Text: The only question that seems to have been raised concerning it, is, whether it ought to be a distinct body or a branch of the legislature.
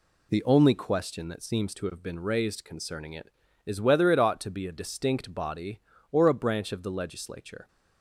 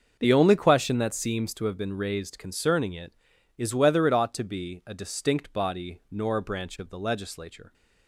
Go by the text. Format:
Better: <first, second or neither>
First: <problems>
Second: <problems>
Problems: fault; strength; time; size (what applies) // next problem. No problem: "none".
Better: first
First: none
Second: starts louder than the rest; until 1.2 s; 6.5 dB // says "nor" for "or"; at 6.1 s